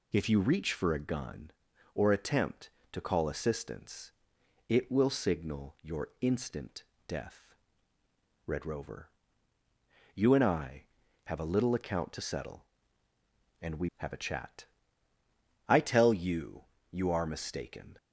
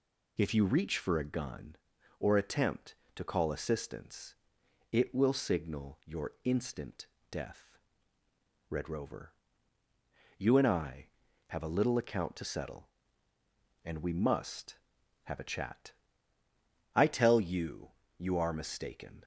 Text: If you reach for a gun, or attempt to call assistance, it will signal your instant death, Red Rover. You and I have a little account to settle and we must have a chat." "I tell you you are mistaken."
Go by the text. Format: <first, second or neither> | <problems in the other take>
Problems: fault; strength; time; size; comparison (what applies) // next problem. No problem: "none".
second | pauses between "instant" and "death"; slight; at 6.8 s; 0.24 s long; slight in the second // skips "must"; at 13.9 s // pauses between "you" and "you"; slight; at 16.6 s; 0.26 s long; slight in the second